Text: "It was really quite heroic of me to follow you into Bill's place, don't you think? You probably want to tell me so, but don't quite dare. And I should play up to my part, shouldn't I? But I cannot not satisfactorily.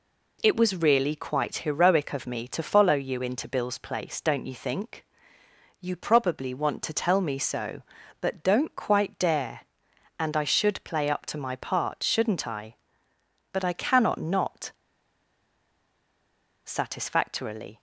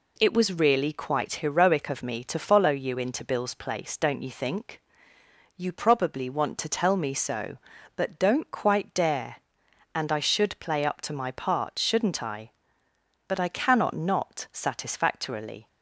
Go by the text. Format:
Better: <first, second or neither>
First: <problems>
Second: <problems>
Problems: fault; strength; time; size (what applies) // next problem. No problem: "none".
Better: second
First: pauses between "not" and "satisfactorily"; strong; at 14.7 s; 1.9 s long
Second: none